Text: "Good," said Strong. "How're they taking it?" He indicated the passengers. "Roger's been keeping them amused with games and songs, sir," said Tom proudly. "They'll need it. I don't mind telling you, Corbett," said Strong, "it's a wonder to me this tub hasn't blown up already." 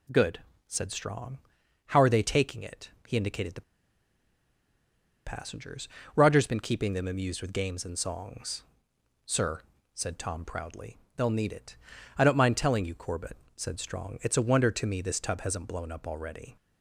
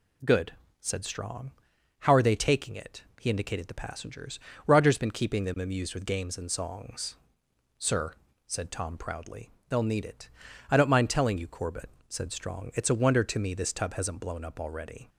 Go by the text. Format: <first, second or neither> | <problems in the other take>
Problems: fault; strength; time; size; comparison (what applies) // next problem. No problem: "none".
second | pauses between "the" and "passengers"; strong; at 3.6 s; 1.6 s long